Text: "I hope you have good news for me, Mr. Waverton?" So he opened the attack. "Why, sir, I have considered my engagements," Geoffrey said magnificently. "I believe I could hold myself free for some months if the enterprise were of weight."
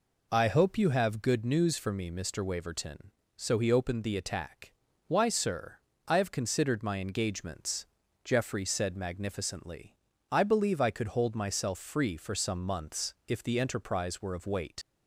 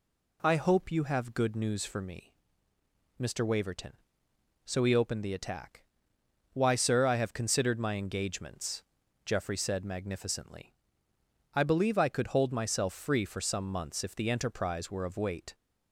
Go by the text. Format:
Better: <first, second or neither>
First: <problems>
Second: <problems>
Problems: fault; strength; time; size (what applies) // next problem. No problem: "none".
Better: second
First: leaves "weight" unfinished; at 14.8 s; 95 ms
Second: none